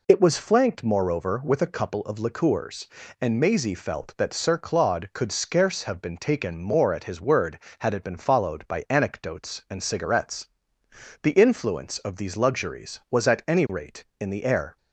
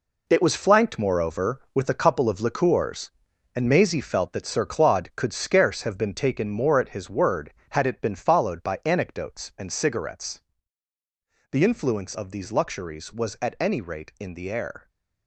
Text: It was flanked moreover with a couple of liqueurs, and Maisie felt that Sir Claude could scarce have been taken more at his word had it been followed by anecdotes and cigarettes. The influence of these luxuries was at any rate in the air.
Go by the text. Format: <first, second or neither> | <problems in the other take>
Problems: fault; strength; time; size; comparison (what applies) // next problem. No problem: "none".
first | gets quieter; strong; throughout; 10 dB